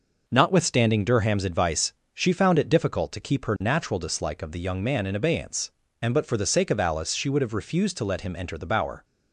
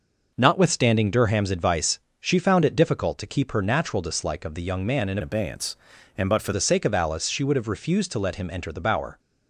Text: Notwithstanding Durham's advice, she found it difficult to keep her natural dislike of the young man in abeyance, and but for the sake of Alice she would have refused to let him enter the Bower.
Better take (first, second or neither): first